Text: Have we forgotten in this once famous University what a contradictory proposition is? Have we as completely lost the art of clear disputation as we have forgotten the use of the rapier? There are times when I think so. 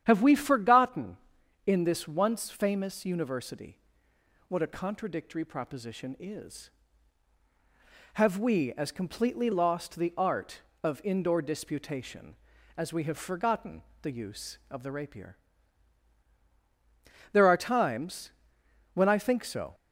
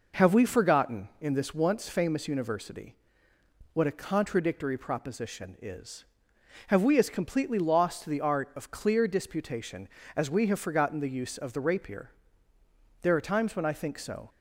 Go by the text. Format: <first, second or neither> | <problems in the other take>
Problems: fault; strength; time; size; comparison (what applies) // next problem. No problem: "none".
second | starts louder than the rest; strong; until 1.0 s; 9.5 dB // pauses between "University" and "what"; noticeable; at 3.7 s; 0.70 s long; noticeable in the second // says "indoor" for "clear"; at 11.0 s // pauses between "forgotten" and "the"; slight; at 13.8 s; 0.20 s long // pauses between "times" and "when"; noticeable; at 18.3 s; 0.64 s long